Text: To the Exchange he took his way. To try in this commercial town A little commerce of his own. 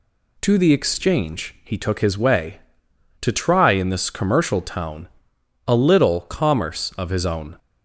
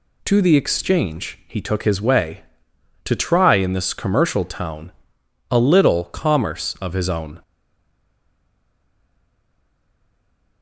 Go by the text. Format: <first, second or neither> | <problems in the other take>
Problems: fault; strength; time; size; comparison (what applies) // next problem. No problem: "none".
first | pauses between "town" and "A"; noticeable; at 4.9 s; 0.58 s long; noticeable in the first // stays silent after the last word; strong; from 7.4 s on; 3.2 s long